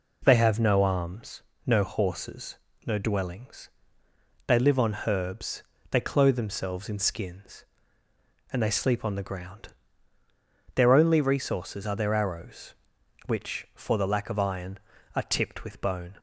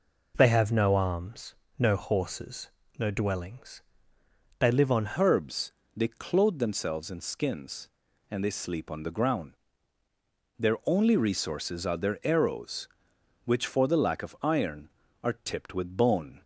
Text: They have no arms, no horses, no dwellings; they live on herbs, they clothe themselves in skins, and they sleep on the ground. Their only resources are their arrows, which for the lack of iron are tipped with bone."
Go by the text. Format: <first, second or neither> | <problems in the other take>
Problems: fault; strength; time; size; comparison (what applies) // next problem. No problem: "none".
first | changes voice at "herbs"; from 5.1 s on; 11.3 s long